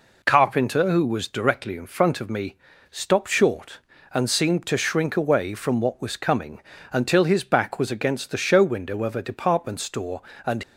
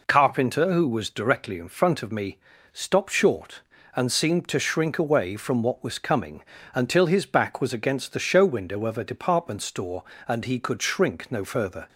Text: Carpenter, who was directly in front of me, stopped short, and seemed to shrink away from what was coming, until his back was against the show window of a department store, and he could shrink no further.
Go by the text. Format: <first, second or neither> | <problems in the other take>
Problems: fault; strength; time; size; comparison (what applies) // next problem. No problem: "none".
second | stops before "he could shrink no further"; at 10.6 s